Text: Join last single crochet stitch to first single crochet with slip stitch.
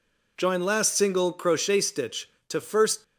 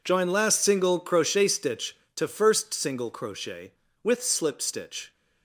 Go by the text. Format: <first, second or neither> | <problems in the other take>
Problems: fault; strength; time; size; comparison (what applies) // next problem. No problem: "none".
second | stops before "single crochet with slip stitch"; at 3.0 s